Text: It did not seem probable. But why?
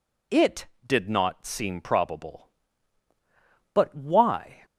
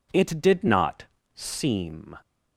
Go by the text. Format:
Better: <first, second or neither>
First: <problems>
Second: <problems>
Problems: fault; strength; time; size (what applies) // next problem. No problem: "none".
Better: first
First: none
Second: pauses between "not" and "seem"; slight; at 1.0 s; 0.30 s long // stops before "probable But why"; at 2.2 s